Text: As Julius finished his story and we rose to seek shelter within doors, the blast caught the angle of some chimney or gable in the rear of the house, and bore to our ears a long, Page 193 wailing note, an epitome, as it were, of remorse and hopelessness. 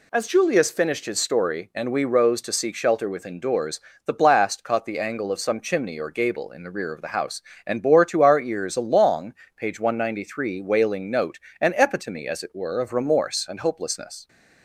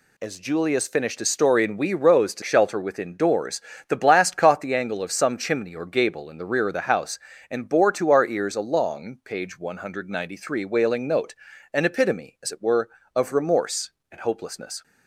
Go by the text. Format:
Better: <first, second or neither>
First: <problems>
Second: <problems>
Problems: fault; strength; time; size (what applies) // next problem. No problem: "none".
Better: first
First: none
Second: skips "seek"; at 2.4 s